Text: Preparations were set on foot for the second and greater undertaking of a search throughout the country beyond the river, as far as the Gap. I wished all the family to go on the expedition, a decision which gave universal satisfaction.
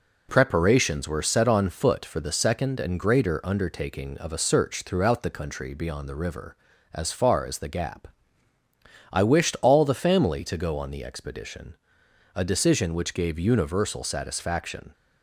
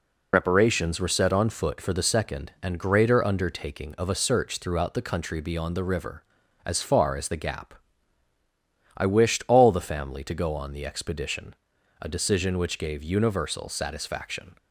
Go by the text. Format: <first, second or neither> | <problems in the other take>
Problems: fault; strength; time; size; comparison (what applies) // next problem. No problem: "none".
first | loses the start of "Preparations"; at 0.3 s; 60 ms